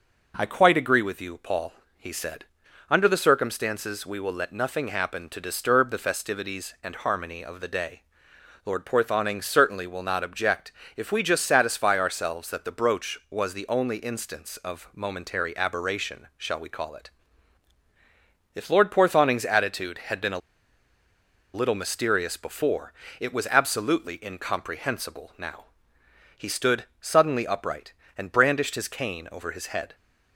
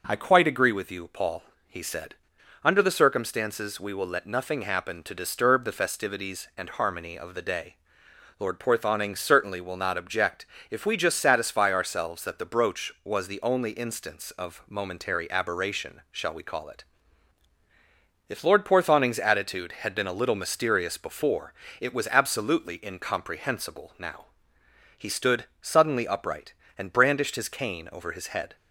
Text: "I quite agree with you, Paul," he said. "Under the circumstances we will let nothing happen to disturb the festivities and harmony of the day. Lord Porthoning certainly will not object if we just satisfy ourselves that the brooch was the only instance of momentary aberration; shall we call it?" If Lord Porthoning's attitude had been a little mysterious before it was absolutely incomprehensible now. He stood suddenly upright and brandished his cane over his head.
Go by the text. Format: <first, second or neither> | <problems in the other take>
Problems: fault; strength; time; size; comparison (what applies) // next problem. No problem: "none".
second | pauses between "object" and "if"; slight; at 10.7 s; 0.24 s long; slight in the second // pauses between "a" and "little"; at 20.3 s; 1.1 s long // pauses between "before" and "it"; slight; at 22.9 s; 0.26 s long; slight in the second // pauses between "stood" and "suddenly"; slight; at 26.8 s; 0.16 s long; slight in the second